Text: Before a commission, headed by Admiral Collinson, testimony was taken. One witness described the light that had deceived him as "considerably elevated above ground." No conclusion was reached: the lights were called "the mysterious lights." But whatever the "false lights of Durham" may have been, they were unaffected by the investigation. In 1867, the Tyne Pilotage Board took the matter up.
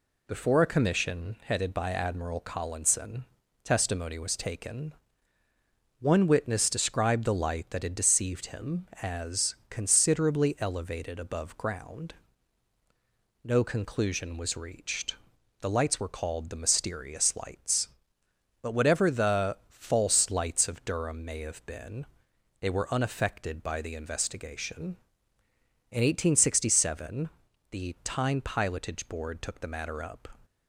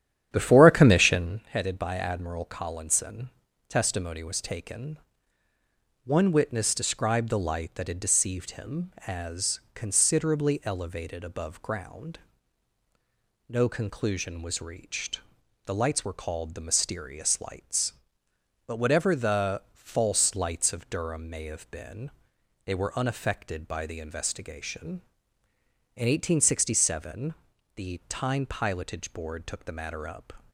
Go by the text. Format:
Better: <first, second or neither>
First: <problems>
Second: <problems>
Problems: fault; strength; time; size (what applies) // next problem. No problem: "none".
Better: first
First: none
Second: starts louder than the rest; strong; until 1.4 s; 10.5 dB